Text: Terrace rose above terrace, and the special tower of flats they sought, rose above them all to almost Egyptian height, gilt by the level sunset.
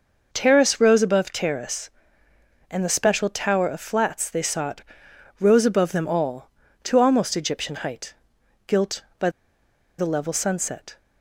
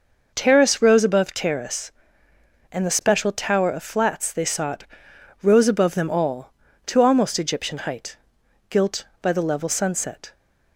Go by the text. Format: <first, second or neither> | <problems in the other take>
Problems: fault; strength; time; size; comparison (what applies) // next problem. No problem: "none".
second | pauses between "by" and "the"; noticeable; at 9.2 s; 0.69 s long